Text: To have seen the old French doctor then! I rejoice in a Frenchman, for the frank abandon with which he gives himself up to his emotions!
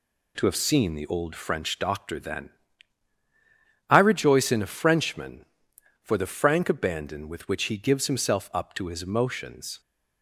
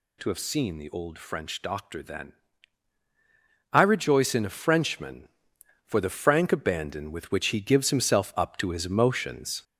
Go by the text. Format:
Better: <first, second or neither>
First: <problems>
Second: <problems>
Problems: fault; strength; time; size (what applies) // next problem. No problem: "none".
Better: first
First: none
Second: gets louder; noticeable; throughout; 4.5 dB